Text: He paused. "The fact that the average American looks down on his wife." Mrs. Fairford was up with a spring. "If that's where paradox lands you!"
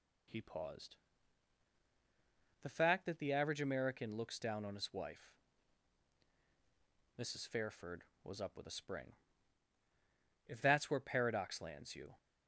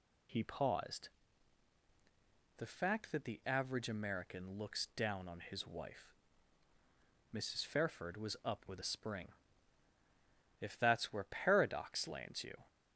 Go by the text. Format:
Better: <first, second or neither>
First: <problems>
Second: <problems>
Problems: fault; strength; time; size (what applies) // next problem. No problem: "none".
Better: neither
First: none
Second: none